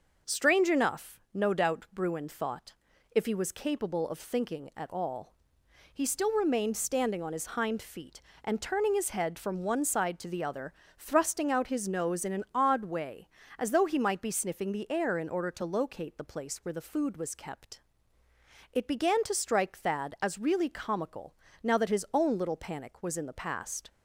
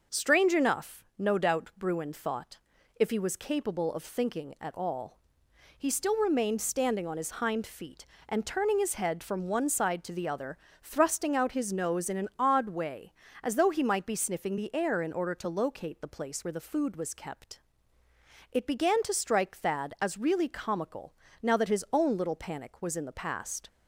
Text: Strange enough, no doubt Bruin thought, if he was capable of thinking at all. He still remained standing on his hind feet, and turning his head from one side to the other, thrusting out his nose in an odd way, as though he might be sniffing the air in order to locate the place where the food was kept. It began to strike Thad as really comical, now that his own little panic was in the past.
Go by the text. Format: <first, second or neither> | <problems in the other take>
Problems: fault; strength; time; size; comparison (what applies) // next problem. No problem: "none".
neither | none